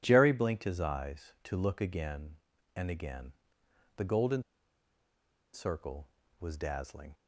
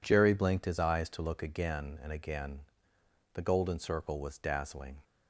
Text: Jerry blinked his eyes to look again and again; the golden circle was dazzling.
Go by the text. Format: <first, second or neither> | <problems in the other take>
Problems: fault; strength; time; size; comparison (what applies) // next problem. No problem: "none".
second | pauses between "golden" and "circle"; at 4.4 s; 1.1 s long